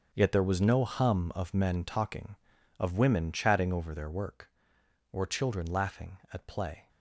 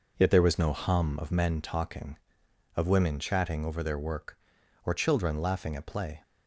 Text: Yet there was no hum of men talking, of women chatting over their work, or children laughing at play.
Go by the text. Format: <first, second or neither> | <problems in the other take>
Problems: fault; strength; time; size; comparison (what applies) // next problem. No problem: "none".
second | gets quieter; strong; throughout; 12.5 dB